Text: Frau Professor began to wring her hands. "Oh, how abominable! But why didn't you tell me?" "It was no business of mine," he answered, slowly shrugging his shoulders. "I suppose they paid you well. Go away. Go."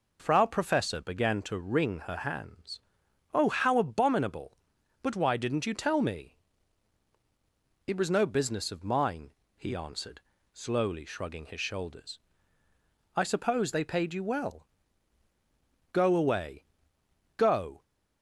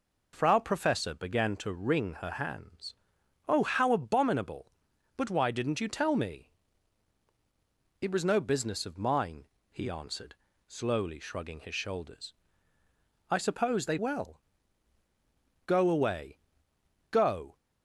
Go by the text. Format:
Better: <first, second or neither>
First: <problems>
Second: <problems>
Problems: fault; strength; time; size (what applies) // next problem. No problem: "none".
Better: first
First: none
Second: skips "paid you"; at 13.9 s